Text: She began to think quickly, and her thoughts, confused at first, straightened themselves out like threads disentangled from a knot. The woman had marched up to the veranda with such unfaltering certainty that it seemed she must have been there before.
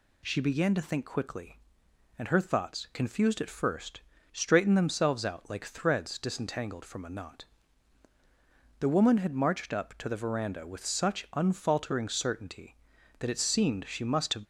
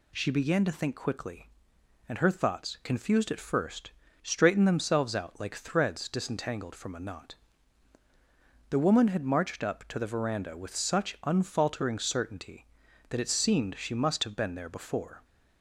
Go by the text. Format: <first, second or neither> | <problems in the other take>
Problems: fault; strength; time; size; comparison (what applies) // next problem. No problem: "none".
second | stops before "been there before"; at 14.4 s